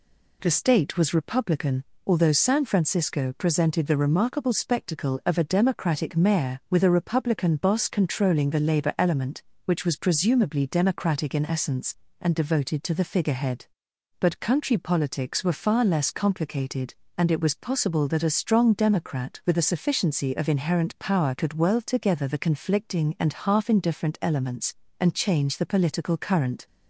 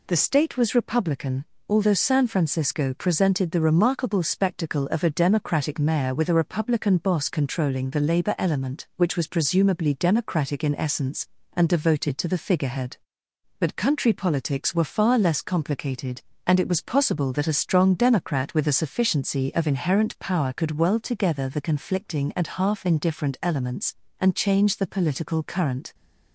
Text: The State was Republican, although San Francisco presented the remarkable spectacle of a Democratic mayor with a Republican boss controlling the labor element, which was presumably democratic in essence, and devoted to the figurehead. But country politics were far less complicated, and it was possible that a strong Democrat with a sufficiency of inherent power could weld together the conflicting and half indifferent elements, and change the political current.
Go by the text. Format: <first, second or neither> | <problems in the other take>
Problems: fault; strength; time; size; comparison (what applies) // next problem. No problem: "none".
neither | none